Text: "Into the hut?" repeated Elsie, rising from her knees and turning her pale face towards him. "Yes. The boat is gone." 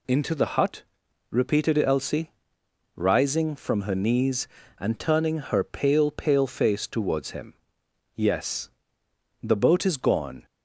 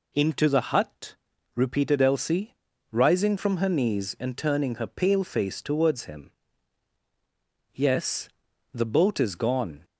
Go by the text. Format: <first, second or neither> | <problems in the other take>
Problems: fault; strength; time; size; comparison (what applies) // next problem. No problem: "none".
second | says "pale" twice; at 6.1 s